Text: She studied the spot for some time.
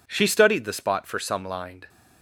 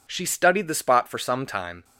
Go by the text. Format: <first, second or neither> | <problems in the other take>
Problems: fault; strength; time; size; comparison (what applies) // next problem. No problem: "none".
second | says "lined" for "time"; at 1.4 s